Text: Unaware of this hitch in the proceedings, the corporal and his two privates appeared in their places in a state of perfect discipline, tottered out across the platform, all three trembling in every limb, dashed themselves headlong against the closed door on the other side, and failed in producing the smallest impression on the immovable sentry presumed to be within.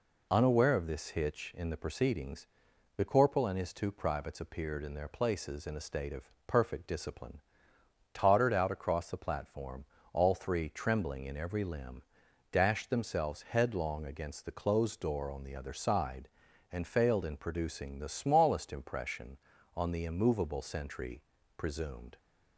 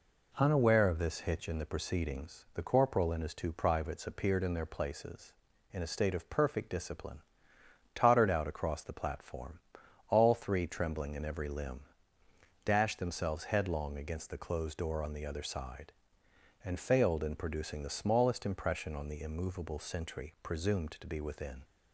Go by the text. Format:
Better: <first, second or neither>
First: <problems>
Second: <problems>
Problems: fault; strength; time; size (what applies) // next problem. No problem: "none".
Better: second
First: pauses between "of" and "perfect"; slight; at 6.2 s; 0.16 s long // pauses between "sentry" and "presumed"; slight; at 21.2 s; 0.36 s long // stops before "to be within"; at 22.1 s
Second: none